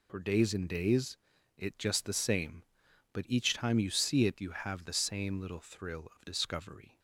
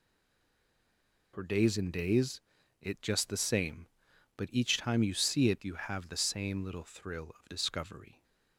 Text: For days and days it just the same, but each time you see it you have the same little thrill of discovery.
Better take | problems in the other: first | stays silent before the first word; noticeable; until 1.3 s; 1.3 s long // pauses between "days" and "it"; at 2.4 s; 0.40 s long; also in the first

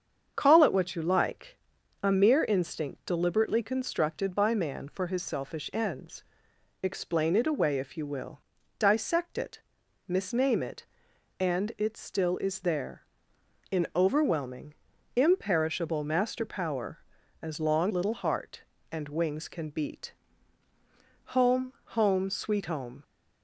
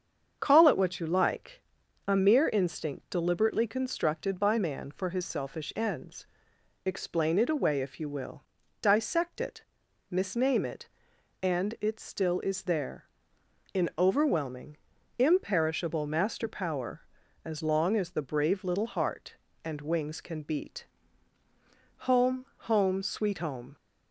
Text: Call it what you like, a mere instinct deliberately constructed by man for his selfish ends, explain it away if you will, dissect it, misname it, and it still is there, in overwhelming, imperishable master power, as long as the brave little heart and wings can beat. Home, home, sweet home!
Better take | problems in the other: second | starts louder than the rest; strong; until 1.3 s; 7.5 dB; strong in the second // skips "as the brave"; at 17.9 s

